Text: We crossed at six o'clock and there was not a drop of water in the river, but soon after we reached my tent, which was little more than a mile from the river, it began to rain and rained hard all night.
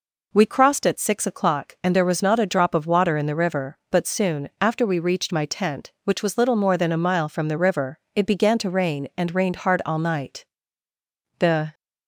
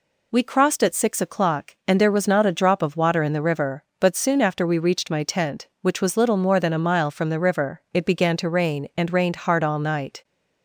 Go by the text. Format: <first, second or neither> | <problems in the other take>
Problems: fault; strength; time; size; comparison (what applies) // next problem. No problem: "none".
second | goes on to say "The"; slight; from 11.3 s on; 0.34 s long